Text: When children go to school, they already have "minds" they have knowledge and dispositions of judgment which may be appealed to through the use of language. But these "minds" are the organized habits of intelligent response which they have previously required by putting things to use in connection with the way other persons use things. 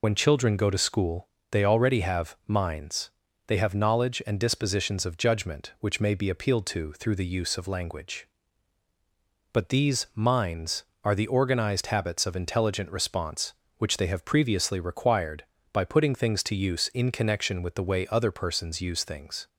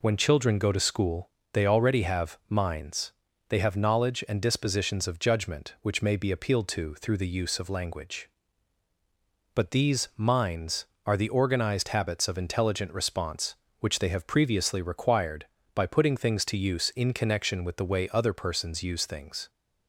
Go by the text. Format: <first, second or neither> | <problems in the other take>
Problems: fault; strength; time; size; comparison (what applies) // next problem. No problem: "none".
second | loses the start of "When"; at 0.0 s; 40 ms // pauses between "minds" and "they"; at 3.0 s; 0.38 s long; also in the second